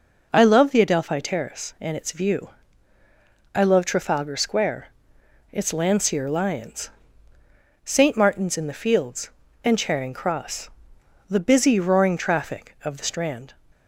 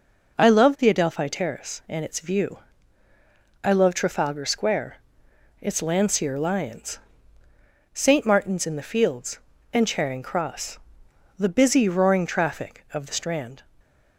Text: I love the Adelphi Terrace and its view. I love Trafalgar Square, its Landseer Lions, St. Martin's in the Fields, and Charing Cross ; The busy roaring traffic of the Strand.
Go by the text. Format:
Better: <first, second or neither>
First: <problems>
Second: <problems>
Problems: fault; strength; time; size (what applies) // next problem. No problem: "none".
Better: neither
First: none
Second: none